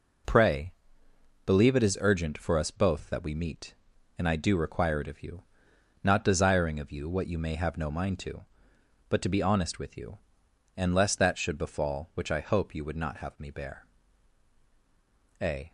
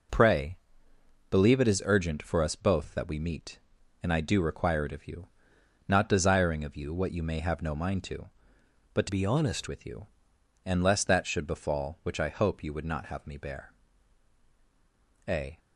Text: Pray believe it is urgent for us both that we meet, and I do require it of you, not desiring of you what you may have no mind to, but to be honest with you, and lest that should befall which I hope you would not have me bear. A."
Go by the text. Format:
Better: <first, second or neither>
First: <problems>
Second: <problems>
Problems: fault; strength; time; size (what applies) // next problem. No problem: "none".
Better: first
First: pauses between "Pray" and "believe"; noticeable; at 0.7 s; 0.74 s long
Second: pauses between "Pray" and "believe"; noticeable; at 0.5 s; 0.74 s long // changes voice from "be" to "honest"; from 9.0 to 9.6 s; 0.6 s long